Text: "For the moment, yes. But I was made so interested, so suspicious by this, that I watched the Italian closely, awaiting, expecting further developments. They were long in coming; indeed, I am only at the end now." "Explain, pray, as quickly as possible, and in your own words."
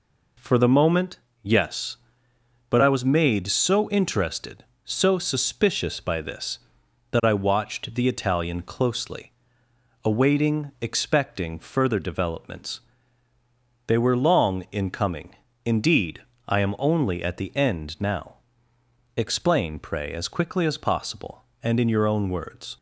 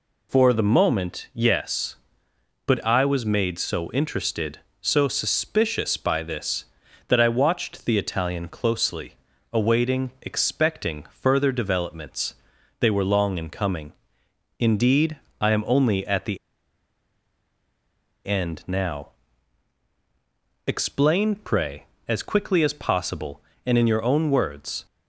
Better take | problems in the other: first | pauses between "the" and "end"; strong; at 16.3 s; 1.8 s long

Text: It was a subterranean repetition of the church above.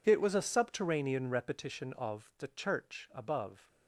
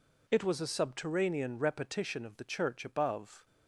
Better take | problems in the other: neither | none

